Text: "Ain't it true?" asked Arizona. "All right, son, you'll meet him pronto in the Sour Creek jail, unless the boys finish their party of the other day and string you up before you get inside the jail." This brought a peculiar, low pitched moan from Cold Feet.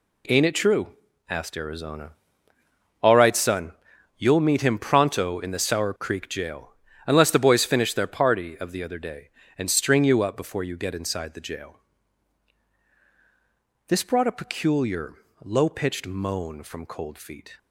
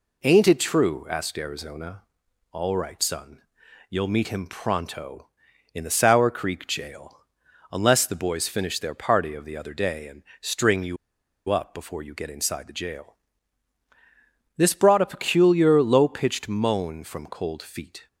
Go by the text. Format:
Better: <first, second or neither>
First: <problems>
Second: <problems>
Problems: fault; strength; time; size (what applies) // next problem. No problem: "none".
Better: first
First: none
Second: pauses between "and" and "string"; slight; at 10.2 s; 0.18 s long // pauses between "you" and "up"; noticeable; at 10.9 s; 0.52 s long